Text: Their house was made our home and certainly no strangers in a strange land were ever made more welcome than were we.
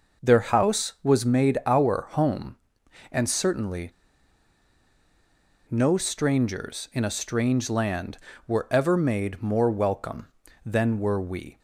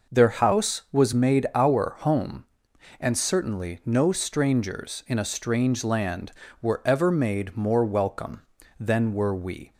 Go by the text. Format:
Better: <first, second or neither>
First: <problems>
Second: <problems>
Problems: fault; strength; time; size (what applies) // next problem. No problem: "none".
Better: second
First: pauses between "certainly" and "no"; strong; at 3.9 s; 1.7 s long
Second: none